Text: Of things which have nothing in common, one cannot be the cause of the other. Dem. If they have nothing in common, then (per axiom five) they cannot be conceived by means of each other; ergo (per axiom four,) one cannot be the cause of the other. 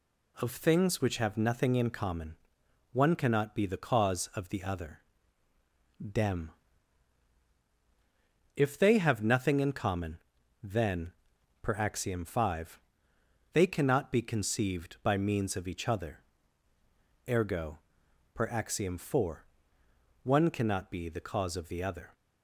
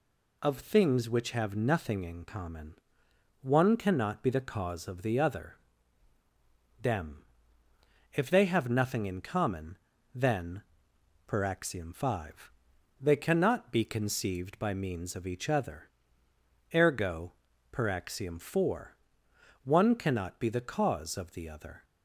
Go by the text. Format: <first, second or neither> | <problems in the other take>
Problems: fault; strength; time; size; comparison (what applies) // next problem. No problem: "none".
neither | none